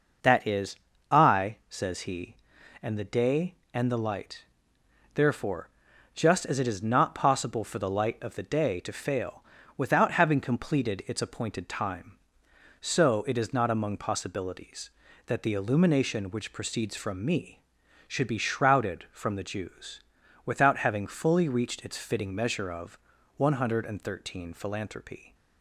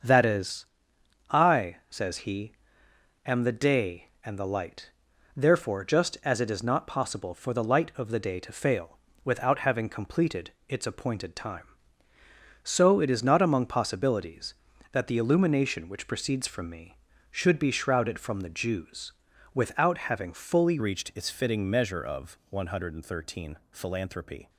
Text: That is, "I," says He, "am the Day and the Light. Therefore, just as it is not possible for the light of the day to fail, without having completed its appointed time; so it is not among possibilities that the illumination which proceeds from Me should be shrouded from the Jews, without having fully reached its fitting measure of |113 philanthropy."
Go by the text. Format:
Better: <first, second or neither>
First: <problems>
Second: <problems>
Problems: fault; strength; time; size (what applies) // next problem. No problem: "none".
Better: first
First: none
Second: starts louder than the rest; until 1.6 s; 6.5 dB // pauses between "completed" and "its"; slight; at 10.5 s; 0.16 s long // changes voice at "reached"; from 20.7 s on; 3.7 s long